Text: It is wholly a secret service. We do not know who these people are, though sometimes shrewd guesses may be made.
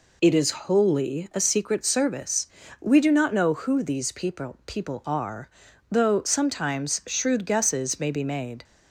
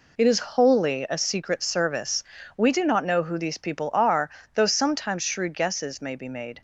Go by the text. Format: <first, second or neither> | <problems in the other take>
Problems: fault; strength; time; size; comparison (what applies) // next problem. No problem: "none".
second | says "people" twice; at 4.6 s